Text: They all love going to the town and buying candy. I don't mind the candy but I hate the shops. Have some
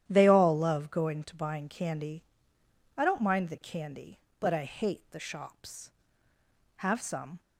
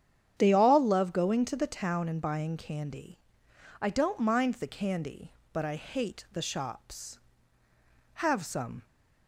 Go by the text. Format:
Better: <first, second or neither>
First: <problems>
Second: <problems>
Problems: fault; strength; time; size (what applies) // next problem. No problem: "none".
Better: second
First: starts louder than the rest; strong; until 1.0 s; 11 dB // skips "the town and"; at 1.3 s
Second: starts louder than the rest; strong; until 1.3 s; 9 dB